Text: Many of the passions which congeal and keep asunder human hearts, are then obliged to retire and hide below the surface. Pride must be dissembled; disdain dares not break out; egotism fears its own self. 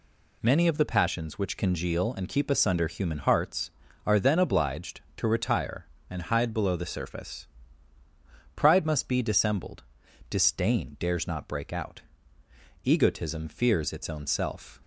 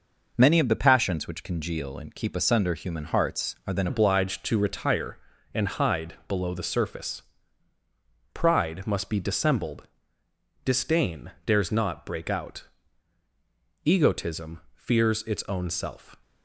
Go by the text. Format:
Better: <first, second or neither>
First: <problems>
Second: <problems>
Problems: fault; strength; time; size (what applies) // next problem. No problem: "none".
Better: first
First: none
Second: changes voice at "obliged"; from 3.8 s on; 12.3 s long // pauses between "disdain" and "dares"; slight; at 11.3 s; 0.16 s long